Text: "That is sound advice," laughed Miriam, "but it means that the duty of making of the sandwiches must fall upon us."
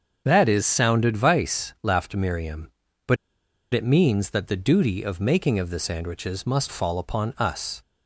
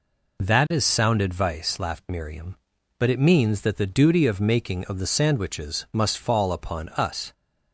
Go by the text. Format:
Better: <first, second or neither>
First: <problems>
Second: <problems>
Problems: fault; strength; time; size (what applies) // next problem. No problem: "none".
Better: second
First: starts louder than the rest; until 1.2 s; 7 dB // pauses between "but" and "it"; noticeable; at 3.1 s; 0.56 s long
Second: none